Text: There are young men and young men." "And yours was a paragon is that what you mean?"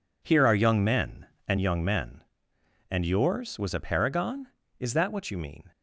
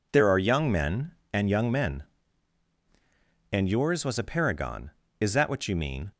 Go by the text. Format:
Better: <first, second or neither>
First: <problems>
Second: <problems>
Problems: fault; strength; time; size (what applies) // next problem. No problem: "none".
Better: second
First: says "Here" for "There"; at 0.2 s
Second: none